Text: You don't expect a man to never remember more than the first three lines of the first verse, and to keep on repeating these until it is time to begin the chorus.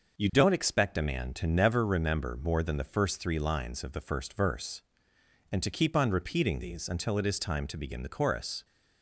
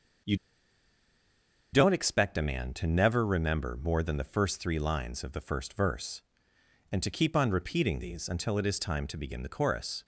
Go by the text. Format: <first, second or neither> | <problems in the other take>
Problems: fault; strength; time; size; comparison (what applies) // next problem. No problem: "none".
first | starts louder than the rest; noticeable; until 2.6 s; 6 dB; noticeable in the first // pauses between "You" and "don't"; strong; at 0.3 s; 1.3 s long